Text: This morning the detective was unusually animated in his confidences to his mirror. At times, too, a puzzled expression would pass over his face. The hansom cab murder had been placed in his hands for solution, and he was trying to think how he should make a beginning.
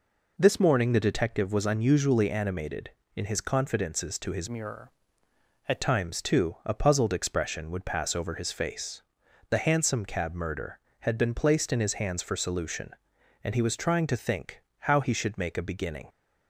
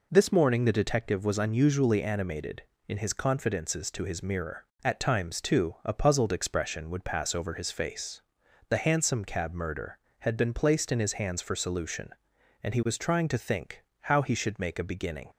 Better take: second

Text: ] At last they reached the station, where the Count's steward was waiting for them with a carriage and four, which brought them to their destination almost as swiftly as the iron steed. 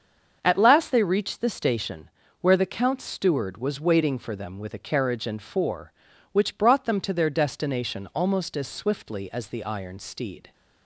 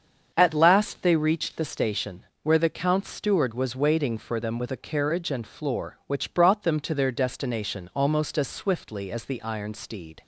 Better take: first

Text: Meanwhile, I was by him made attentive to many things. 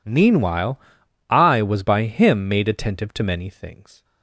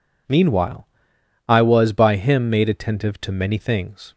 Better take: neither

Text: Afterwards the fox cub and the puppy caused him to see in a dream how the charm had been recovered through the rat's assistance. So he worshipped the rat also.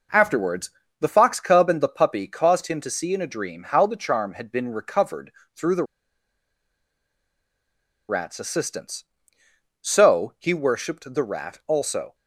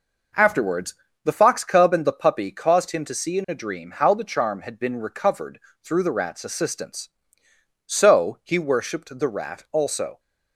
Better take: second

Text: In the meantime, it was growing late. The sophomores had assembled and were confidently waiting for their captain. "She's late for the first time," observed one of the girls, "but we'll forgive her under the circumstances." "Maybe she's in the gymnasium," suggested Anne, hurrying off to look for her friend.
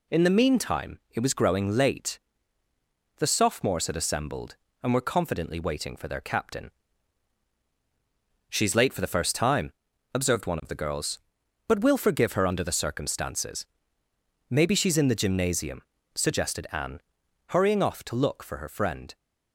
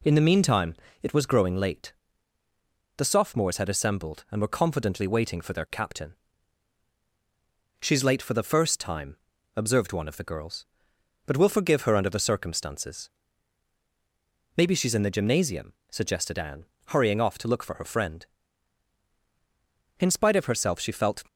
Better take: first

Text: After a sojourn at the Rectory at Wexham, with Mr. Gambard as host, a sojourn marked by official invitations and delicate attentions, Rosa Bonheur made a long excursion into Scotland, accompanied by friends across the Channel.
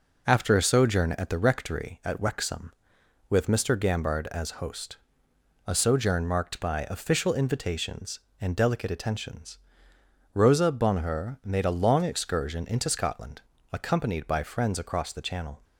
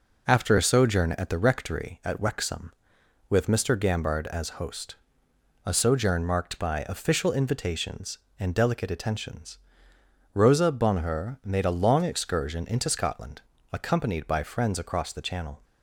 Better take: neither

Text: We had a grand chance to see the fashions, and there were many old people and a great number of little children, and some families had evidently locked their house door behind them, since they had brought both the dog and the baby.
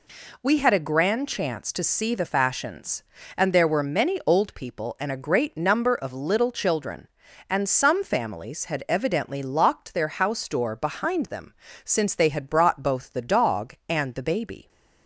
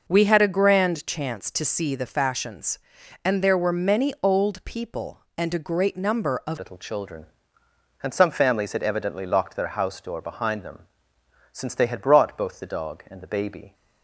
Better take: first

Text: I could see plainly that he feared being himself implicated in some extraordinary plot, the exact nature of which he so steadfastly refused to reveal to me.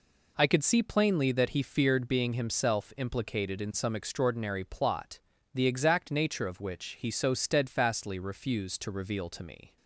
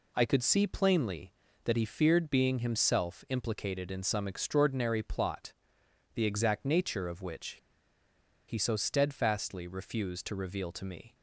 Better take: first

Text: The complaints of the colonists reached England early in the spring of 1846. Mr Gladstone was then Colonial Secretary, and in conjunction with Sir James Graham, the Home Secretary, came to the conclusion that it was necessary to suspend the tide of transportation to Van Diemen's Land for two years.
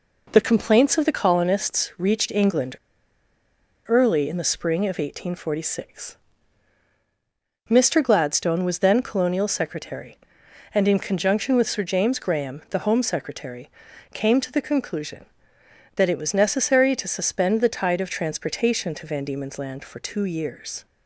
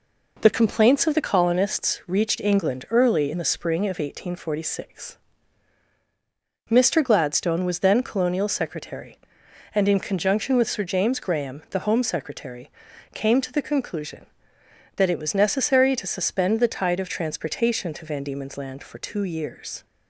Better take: second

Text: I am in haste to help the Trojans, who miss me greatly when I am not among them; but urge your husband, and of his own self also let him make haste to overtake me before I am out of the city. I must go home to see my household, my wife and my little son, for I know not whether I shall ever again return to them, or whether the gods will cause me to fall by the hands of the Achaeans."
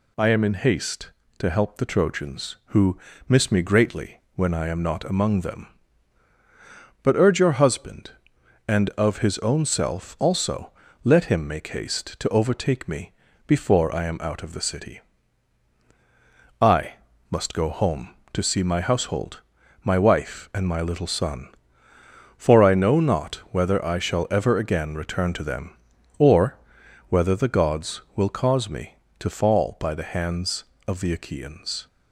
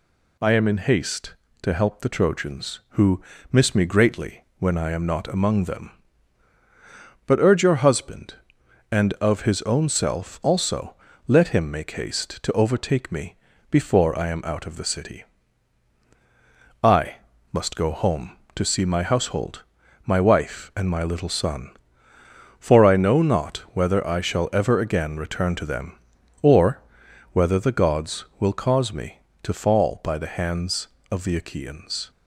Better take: neither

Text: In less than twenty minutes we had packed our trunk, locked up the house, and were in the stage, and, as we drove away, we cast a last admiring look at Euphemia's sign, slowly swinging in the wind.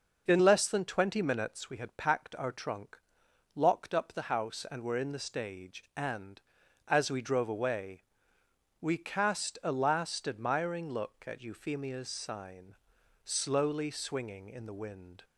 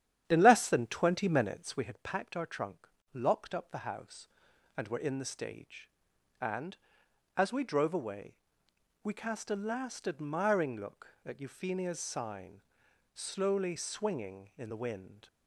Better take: first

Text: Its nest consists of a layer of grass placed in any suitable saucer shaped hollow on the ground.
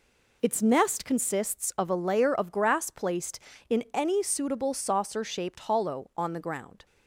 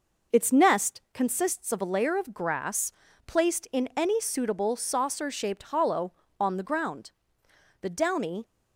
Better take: first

